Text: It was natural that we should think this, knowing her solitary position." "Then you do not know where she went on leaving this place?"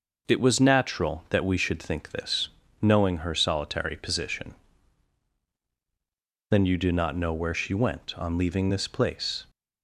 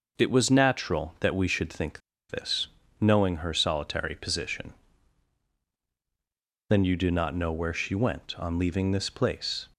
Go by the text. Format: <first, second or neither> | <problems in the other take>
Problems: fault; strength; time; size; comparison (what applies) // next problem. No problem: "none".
first | pauses between "think" and "this"; slight; at 1.9 s; 0.29 s long